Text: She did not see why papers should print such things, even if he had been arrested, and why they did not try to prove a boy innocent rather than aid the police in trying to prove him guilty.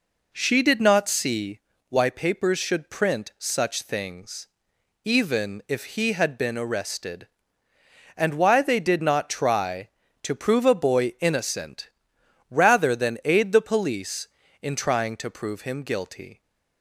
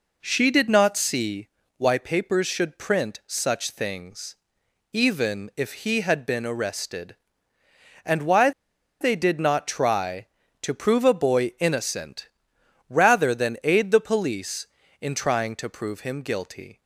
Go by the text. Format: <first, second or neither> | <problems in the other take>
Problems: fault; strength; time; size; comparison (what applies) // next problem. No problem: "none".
first | pauses between "see" and "why"; slight; at 1.4 s; 0.30 s long; slight in the first // pauses between "why" and "they"; noticeable; at 8.5 s; 0.49 s long // pauses between "innocent" and "rather"; noticeable; at 12.2 s; 0.58 s long; noticeable in the first